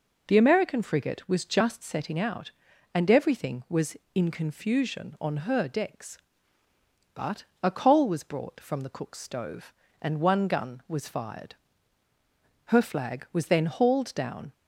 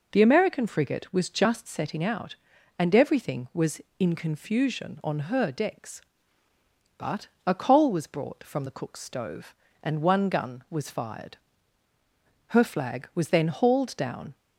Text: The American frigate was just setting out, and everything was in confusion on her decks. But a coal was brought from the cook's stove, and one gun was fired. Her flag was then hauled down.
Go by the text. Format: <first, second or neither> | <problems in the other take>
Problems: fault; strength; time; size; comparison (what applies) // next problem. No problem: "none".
neither | pauses between "But" and "a"; slight; the same in both